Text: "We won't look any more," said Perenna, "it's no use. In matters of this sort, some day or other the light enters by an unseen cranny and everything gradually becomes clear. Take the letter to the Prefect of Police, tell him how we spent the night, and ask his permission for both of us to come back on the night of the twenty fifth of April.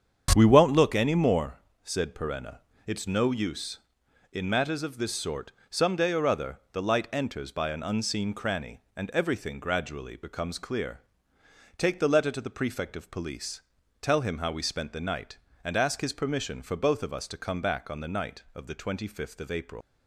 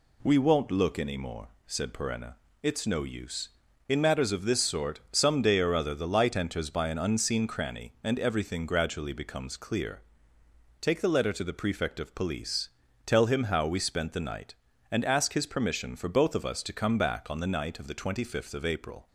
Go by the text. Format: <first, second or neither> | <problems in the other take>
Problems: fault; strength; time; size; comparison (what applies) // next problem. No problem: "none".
second | starts louder than the rest; strong; until 1.3 s; 8 dB // leaves "April" unfinished; at 19.8 s; 85 ms